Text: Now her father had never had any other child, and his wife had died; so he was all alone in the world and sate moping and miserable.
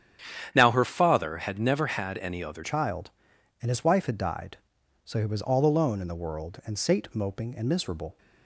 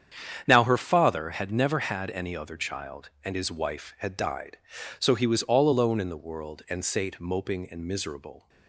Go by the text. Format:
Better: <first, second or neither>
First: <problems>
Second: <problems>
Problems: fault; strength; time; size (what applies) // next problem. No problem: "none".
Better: second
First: starts louder than the rest; strong; until 1.5 s; 9.5 dB // changes voice at "child"; from 2.6 s on; 5.5 s long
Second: starts louder than the rest; strong; until 1.4 s; 8.5 dB